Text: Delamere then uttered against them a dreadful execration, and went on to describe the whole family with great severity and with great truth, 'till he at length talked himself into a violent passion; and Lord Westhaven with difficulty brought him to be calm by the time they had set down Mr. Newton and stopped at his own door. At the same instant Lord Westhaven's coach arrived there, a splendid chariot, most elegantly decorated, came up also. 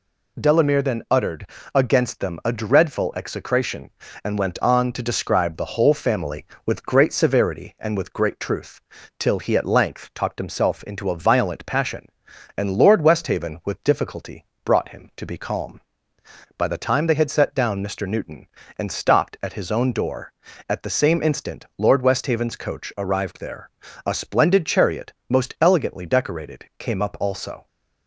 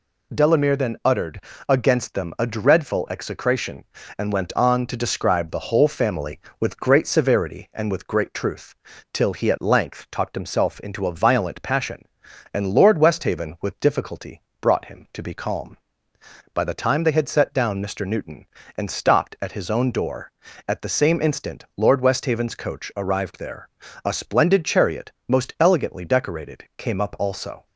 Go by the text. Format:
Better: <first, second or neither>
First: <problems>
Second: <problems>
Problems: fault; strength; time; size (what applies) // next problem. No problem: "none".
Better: neither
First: pauses between "uttered" and "against"; slight; at 1.4 s; 0.26 s long // pauses between "difficulty" and "brought"; slight; at 14.4 s; 0.20 s long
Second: pauses between "uttered" and "against"; slight; at 1.4 s; 0.26 s long // pauses between "difficulty" and "brought"; slight; at 14.4 s; 0.20 s long